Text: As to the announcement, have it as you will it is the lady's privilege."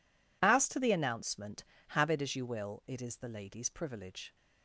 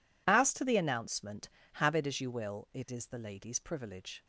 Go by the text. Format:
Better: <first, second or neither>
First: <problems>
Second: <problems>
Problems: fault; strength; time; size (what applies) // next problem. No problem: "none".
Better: neither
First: none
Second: none